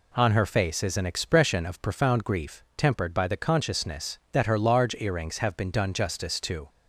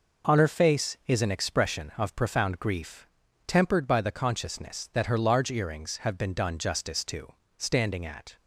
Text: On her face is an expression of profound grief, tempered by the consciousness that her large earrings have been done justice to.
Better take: first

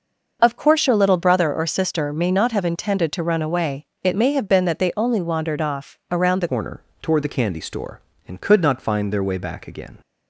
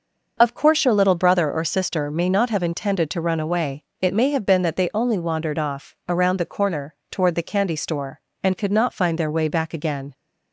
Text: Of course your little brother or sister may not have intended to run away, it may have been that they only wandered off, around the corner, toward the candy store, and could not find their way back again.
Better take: second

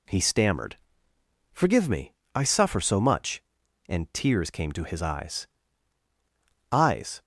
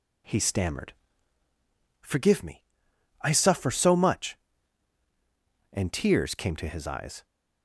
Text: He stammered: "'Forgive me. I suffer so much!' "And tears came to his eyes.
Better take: second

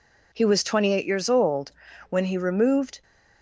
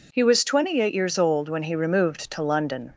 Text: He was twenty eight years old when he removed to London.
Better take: second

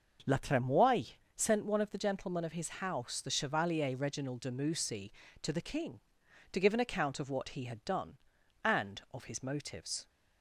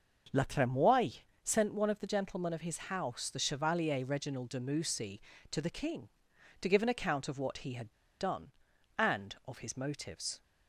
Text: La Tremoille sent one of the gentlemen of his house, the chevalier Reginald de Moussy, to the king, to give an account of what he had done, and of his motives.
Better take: first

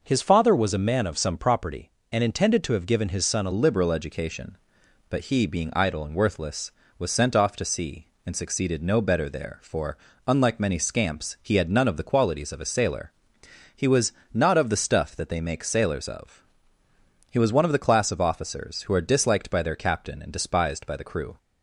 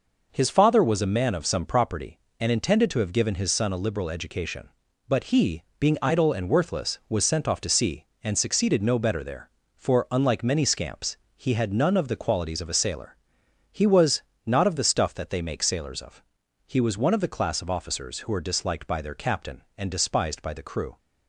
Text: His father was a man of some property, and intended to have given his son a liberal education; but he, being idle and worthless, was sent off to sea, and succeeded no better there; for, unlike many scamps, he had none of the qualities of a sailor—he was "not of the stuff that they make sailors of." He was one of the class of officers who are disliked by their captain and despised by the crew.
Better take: second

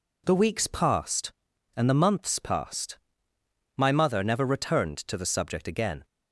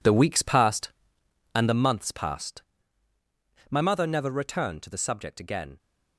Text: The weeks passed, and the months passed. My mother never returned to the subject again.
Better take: first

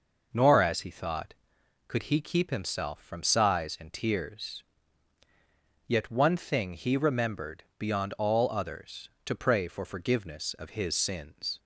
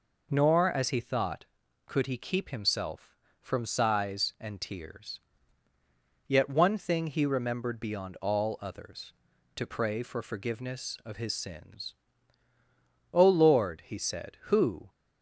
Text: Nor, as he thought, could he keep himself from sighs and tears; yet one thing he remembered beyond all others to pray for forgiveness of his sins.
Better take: first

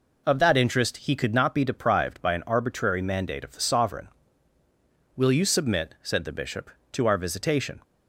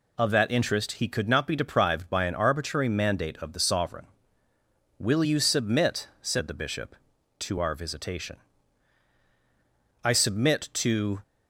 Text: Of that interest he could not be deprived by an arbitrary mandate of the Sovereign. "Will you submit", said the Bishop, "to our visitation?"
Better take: first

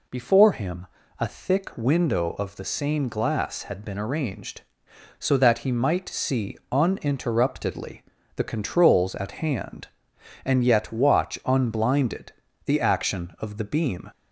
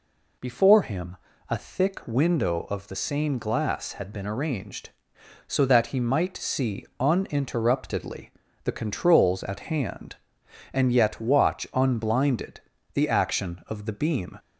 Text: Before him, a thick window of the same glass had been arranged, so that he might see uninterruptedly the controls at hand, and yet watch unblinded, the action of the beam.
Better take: neither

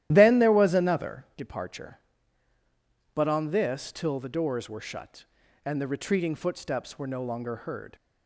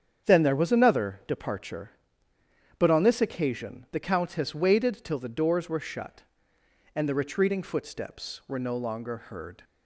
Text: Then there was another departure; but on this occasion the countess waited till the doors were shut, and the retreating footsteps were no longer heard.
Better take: second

